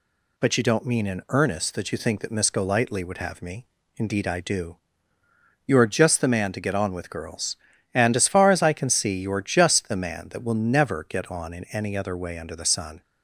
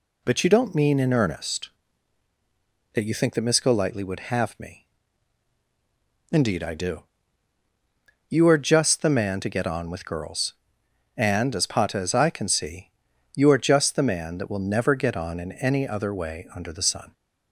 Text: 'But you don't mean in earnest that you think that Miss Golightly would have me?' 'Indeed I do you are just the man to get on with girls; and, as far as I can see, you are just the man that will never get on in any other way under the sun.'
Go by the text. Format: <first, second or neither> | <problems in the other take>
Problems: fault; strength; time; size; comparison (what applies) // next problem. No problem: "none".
first | pauses between "do" and "you"; strong; at 7.0 s; 1.2 s long; noticeable in the first // says "pata" for "far"; at 11.6 s